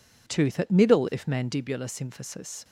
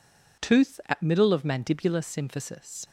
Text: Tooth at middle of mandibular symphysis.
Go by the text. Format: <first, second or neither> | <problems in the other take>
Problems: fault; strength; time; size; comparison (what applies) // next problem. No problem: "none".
second | says "if" for "of"; at 1.1 s